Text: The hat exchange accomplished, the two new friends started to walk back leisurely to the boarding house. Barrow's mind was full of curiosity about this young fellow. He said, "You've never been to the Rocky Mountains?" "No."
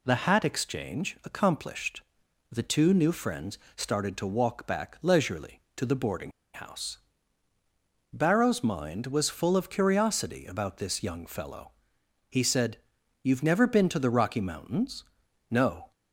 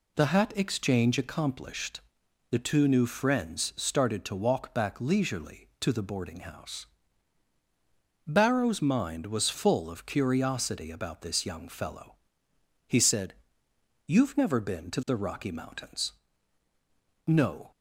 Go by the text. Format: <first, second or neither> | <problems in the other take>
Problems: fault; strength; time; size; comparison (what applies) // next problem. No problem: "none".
second | pauses between "friends" and "started"; slight; at 3.5 s; 0.16 s long // pauses between "boarding" and "house"; slight; at 6.3 s; 0.22 s long